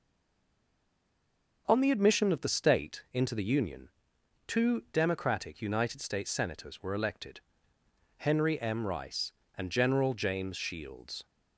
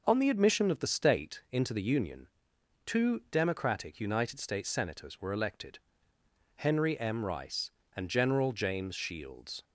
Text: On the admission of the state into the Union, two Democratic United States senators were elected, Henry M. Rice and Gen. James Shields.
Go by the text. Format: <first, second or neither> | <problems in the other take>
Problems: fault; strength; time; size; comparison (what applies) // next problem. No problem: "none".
second | stays silent before the first word; noticeable; until 1.6 s; 1.6 s long